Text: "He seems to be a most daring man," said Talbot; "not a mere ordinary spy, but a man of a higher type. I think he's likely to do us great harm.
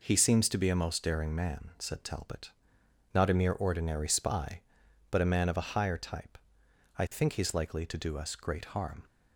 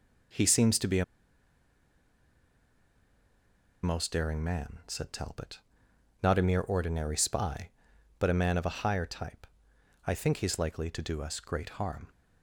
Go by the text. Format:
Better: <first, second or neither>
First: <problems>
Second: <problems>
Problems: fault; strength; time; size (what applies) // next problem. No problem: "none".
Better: first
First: none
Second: pauses between "a" and "most"; strong; at 1.0 s; 2.7 s long